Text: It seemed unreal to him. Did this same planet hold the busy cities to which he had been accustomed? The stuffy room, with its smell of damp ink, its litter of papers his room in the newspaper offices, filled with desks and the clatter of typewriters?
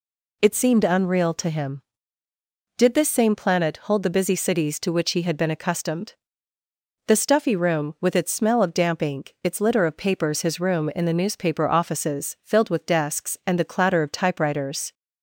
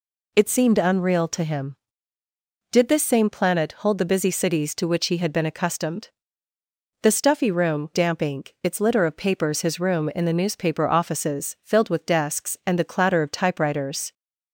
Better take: first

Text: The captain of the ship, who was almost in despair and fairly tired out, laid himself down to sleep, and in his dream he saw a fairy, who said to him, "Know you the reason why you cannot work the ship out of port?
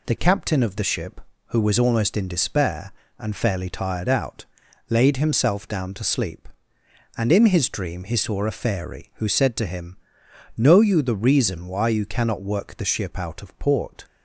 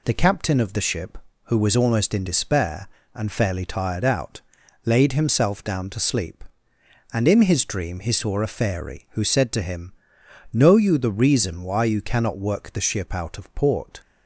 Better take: neither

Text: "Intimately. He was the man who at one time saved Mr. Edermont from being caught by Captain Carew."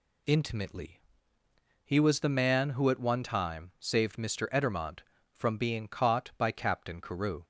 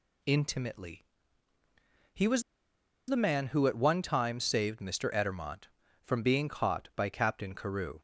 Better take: first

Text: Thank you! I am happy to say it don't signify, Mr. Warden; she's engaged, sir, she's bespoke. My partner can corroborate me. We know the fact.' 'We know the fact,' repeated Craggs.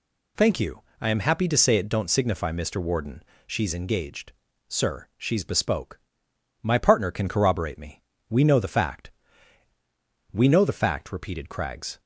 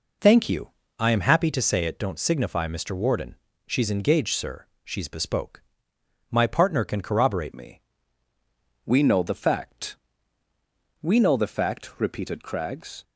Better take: first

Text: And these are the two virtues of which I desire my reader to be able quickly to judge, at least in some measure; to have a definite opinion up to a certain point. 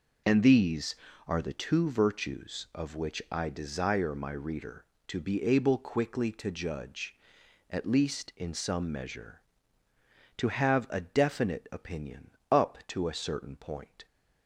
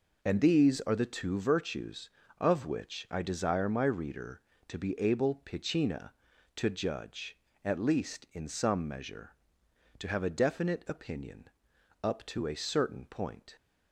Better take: first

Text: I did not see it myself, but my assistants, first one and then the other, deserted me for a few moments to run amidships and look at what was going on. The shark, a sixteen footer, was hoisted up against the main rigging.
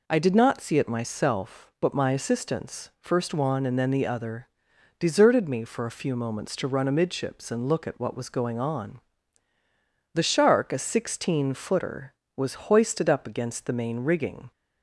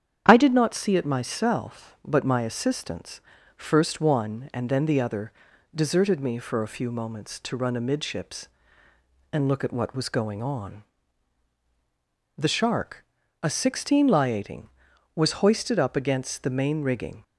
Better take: first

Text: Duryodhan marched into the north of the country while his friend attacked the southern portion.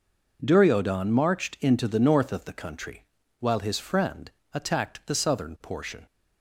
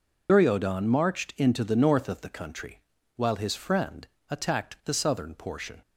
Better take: first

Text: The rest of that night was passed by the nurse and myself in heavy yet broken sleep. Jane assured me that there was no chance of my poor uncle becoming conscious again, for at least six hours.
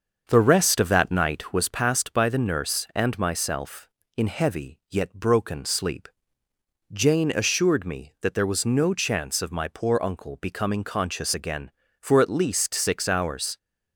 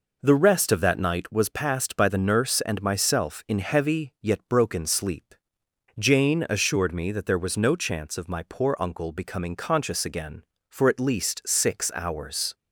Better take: second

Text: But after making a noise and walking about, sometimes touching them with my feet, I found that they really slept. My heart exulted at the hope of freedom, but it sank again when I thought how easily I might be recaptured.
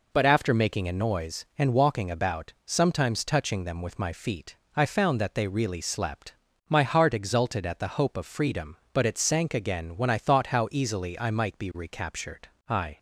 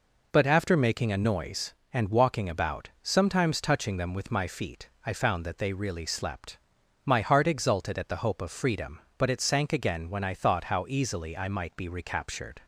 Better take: second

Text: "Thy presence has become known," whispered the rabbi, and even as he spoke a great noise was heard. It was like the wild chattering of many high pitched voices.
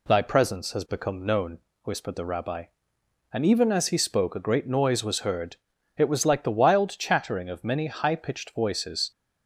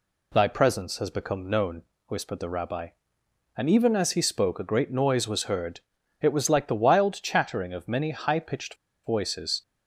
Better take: first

